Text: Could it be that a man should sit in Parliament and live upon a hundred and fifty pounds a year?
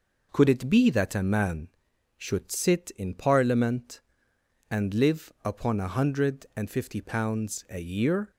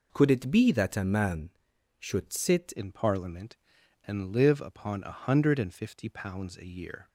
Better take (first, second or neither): first